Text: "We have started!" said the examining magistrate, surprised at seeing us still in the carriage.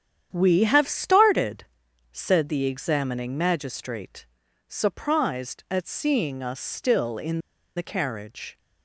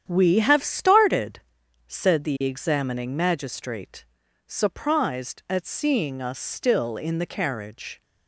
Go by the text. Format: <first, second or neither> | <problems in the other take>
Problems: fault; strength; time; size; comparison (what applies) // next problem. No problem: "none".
second | starts louder than the rest; strong; until 1.3 s; 9 dB; strong in the second // pauses between "in" and "the"; slight; at 7.4 s; 0.35 s long